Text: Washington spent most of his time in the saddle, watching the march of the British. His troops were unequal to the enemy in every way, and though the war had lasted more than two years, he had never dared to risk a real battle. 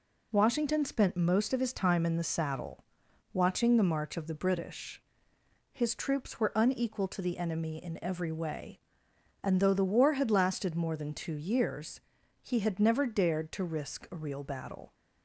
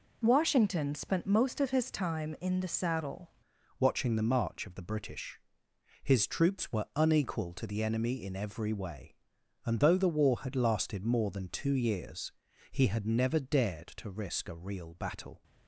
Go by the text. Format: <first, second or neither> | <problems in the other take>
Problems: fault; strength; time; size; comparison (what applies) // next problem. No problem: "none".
first | changes voice at "watching"; from 3.7 s on; 11.7 s long